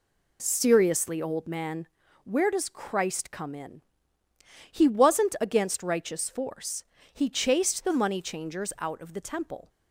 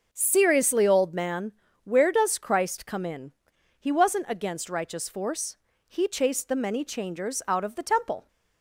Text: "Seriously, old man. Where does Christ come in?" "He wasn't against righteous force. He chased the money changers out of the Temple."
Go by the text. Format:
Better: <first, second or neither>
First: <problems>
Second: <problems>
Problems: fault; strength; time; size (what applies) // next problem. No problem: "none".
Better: first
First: none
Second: says "many" for "money"; at 6.5 s